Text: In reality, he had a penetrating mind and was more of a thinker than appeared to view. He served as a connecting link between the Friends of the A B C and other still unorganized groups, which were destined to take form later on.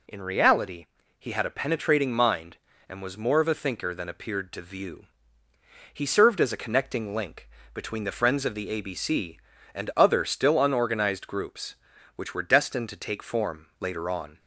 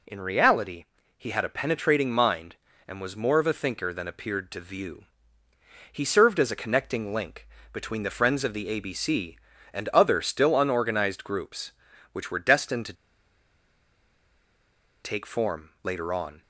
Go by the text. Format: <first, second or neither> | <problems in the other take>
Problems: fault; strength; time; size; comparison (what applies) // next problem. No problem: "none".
first | pauses between "link" and "between"; slight; at 7.4 s; 0.26 s long; slight in the first // pauses between "to" and "take"; strong; at 12.9 s; 2.0 s long